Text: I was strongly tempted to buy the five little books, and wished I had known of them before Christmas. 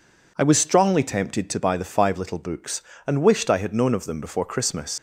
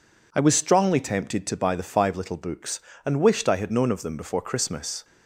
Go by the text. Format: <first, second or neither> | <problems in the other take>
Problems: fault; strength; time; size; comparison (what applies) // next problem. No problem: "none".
second | leaves "Christmas" unfinished; at 4.9 s; 100 ms